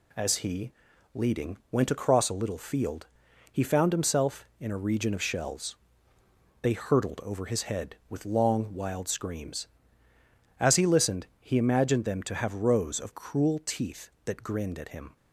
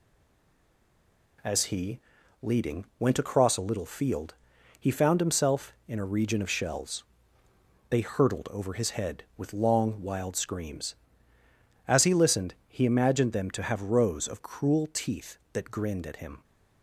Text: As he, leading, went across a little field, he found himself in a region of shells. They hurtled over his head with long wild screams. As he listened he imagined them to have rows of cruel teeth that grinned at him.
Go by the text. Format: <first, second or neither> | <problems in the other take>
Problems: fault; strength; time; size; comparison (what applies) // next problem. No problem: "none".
first | stays silent before the first word; noticeable; until 1.3 s; 1.3 s long